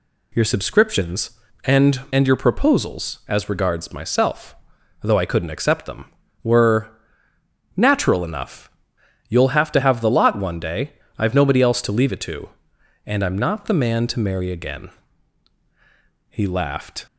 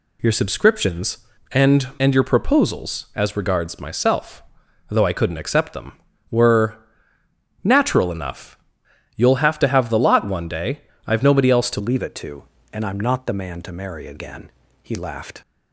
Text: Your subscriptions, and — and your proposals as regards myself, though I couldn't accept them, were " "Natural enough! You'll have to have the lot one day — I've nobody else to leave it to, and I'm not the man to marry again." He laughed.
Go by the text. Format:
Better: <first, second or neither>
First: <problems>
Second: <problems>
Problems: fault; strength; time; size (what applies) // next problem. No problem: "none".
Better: first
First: none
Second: changes voice at "leave"; from 11.7 s on; 3.7 s long